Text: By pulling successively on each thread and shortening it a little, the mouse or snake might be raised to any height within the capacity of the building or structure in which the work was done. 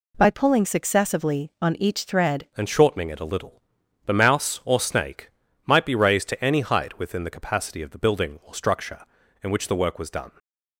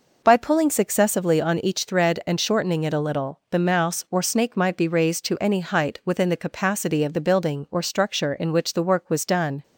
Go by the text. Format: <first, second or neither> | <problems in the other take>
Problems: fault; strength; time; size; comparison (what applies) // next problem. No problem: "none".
second | changes voice at "and"; from 2.5 s on; 7.8 s long // pauses between "snake" and "might"; slight; at 5.2 s; 0.36 s long // stays silent after the last word; slight; from 10.2 s on; 0.5 s long